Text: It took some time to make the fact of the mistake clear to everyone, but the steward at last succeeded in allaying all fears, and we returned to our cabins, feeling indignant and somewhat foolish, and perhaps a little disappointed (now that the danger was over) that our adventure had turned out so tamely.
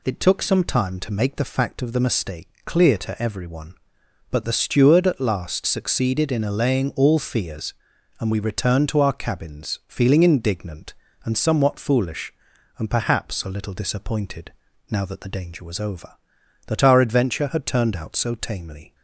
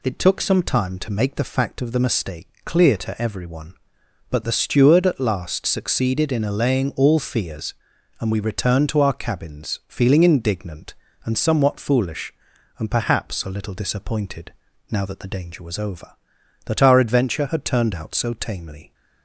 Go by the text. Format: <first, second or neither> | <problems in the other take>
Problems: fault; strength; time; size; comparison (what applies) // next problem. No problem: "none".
neither | pauses between "mistake" and "clear"; slight; the same in both